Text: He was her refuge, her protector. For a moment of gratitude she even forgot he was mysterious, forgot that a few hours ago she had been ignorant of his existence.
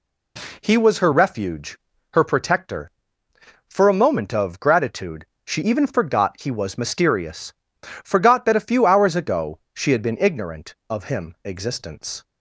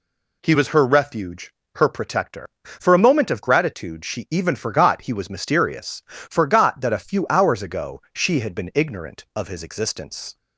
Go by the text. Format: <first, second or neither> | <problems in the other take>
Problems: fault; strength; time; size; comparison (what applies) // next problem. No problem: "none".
second | pauses between "gratitude" and "she"; slight; at 5.2 s; 0.20 s long // pauses between "ago" and "she"; slight; at 9.5 s; 0.16 s long // says "him" for "his"; at 11.0 s